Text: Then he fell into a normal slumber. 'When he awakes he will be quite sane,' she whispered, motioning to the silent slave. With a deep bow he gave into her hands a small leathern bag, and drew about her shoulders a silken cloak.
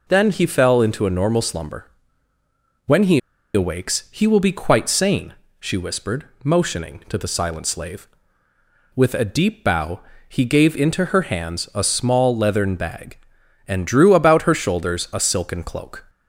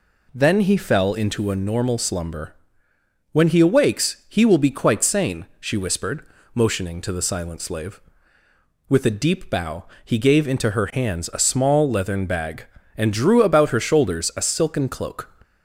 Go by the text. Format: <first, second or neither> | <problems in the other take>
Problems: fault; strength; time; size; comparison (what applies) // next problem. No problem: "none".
second | pauses between "he" and "awakes"; slight; at 3.1 s; 0.35 s long // pauses between "bow" and "he"; slight; at 9.9 s; 0.28 s long; slight in the second